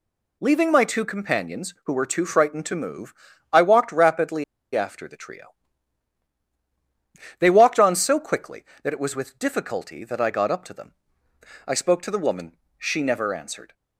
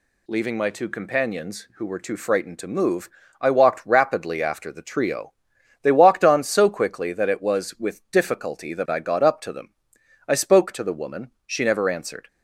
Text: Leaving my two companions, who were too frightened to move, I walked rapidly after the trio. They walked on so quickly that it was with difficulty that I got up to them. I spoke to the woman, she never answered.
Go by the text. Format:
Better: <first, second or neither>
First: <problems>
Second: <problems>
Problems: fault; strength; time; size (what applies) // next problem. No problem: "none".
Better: second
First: pauses between "rapidly" and "after"; slight; at 4.4 s; 0.31 s long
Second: none